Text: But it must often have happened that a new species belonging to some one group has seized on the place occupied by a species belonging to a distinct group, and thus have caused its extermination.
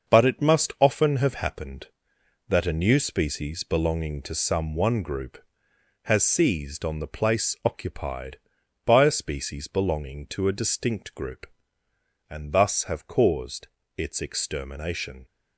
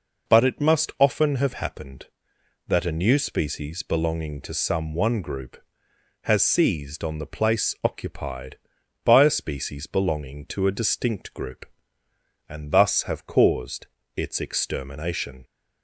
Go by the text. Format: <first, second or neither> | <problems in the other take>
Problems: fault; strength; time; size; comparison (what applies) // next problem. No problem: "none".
second | gets quieter; throughout; 7 dB // pauses between "caused" and "its"; slight; at 13.6 s; 0.30 s long; slight in the second